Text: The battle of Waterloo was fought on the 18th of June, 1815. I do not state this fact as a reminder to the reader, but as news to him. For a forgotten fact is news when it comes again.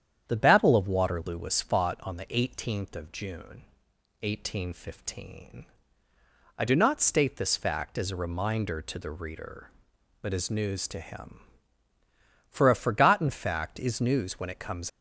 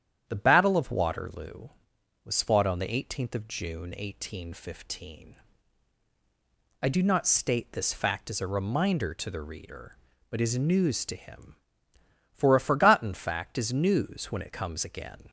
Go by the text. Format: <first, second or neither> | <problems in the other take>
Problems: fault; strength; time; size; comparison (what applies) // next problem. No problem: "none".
second | starts louder than the rest; strong; until 1.2 s; 9 dB; strong in the second // stops before "again"; at 14.8 s